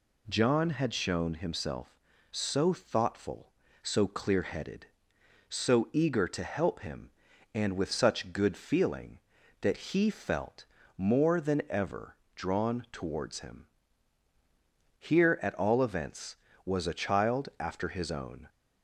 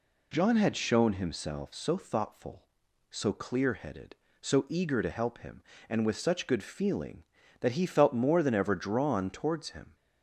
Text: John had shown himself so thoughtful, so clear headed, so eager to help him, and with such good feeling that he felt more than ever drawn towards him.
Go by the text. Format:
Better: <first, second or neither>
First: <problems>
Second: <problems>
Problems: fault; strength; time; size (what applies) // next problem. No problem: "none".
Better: second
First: pauses between "felt" and "more"; slight; at 10.6 s; 0.32 s long // pauses between "ever" and "drawn"; slight; at 12.1 s; 0.20 s long // goes on to say "Here at all events was a child after his own"; strong; from 14.9 s on; 3.5 s long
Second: none